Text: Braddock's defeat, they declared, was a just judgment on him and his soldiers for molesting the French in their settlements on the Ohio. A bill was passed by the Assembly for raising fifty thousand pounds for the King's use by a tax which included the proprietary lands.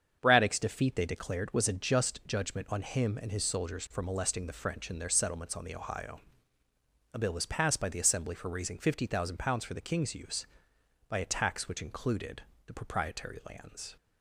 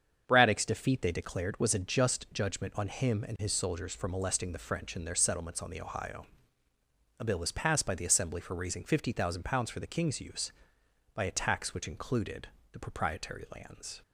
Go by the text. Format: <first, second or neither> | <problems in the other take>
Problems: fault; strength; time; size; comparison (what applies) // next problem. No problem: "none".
neither | starts louder than the rest; strong; the same in both // pauses between "included" and "the"; slight; the same in both